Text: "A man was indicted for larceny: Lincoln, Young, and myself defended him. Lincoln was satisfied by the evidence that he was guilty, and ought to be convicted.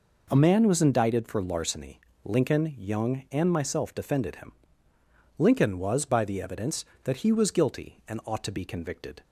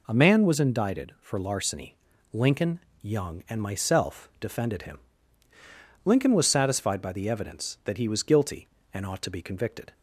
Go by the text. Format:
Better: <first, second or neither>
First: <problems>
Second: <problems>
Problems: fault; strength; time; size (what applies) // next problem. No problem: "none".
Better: second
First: skips "satisfied"; at 6.0 s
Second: none